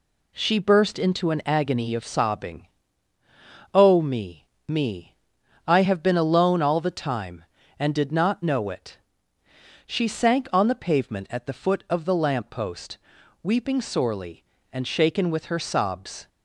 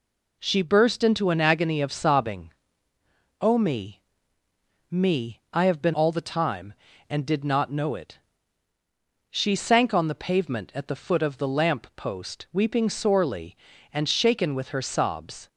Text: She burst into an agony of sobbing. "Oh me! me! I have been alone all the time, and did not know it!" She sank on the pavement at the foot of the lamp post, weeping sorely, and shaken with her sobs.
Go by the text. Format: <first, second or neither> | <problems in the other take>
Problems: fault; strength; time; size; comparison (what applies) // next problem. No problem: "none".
first | skips "alone"; at 5.9 s